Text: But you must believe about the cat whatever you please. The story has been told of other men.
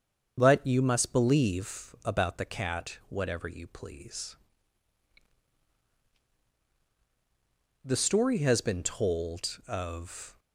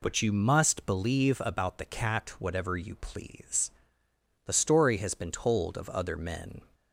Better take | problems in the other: second | starts louder than the rest; until 1.3 s; 7 dB // stops before "other men"; at 10.3 s

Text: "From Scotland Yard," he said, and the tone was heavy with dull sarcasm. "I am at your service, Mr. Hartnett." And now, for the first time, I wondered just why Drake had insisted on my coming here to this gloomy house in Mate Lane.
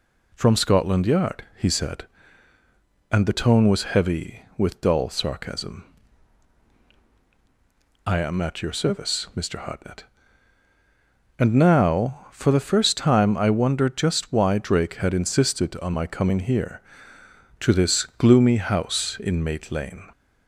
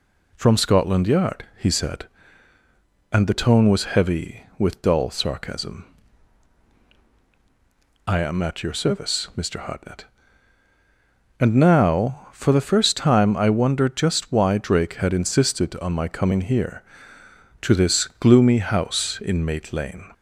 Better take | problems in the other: neither | none

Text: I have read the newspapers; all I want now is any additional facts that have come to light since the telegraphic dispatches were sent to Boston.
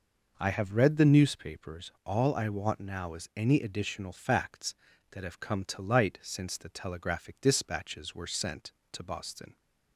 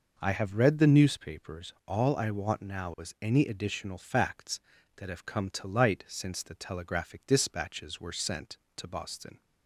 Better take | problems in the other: neither | none

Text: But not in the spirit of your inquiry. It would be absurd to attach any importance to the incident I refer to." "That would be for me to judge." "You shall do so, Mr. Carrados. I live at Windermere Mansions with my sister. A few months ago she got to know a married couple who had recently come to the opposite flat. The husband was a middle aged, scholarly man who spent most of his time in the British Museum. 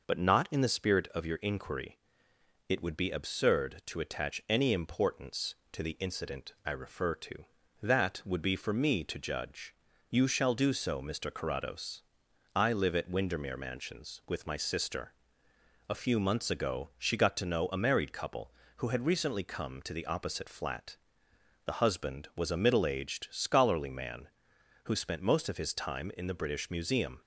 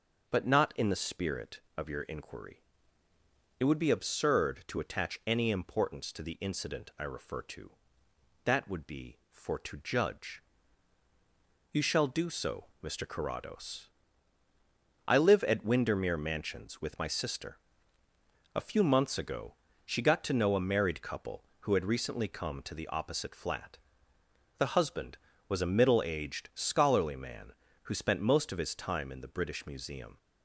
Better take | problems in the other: first | starts louder than the rest; until 1.3 s; 6 dB // skips "me"; at 9.5 s // pauses between "ago" and "she"; slight; at 19.5 s; 0.32 s long

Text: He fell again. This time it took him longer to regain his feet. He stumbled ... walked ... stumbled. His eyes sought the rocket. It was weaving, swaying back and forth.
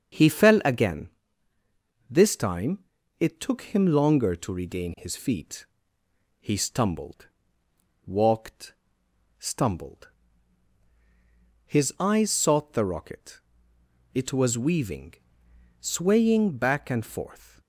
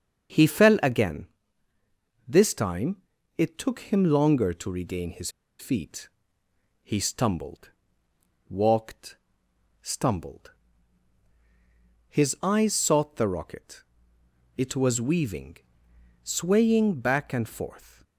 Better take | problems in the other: first | starts louder than the rest; until 2.3 s; 6.5 dB; also in the first // pauses between "time" and "it"; slight; at 3.0 s; 0.36 s long; slight in the first // pauses between "his" and "feet"; slight; at 5.2 s; 0.30 s long

